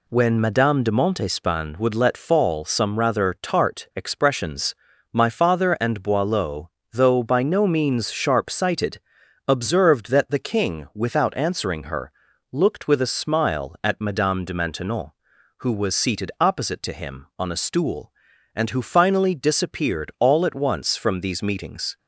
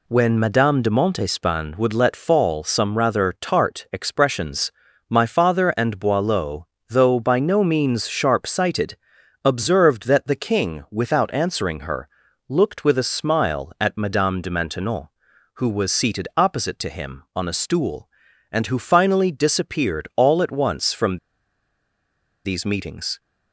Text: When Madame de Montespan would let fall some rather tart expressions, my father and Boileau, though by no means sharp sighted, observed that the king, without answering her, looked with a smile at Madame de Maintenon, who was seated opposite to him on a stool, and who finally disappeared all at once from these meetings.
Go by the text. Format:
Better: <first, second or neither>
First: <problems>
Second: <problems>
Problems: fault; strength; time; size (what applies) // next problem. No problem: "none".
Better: first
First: none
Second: pauses between "from" and "these"; strong; at 21.1 s; 1.2 s long